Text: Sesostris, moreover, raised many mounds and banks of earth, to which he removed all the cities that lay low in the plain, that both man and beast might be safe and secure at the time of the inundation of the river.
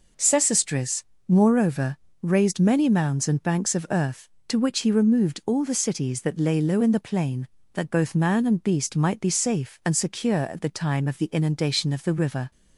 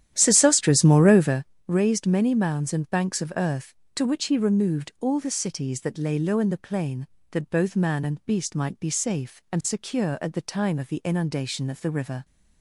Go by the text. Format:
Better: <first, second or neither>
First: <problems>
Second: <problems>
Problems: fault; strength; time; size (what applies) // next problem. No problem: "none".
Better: first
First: none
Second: starts louder than the rest; strong; until 1.5 s; 11 dB